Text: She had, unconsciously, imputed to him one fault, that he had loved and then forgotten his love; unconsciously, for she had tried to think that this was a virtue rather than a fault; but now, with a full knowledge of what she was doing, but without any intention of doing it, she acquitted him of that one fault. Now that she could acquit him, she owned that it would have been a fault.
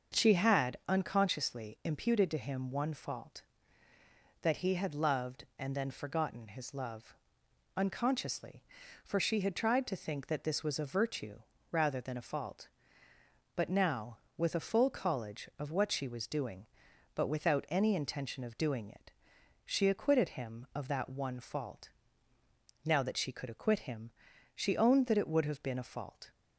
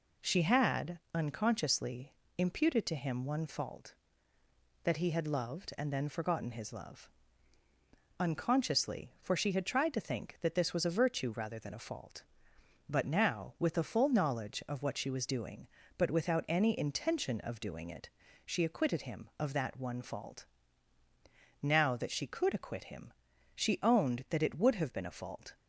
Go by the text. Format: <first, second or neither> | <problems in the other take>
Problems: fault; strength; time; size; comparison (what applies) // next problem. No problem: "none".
second | starts louder than the rest; until 1.2 s; 6.5 dB // pauses between "virtue" and "rather"; slight; at 11.4 s; 0.30 s long // says "college" for "knowledge"; at 14.9 s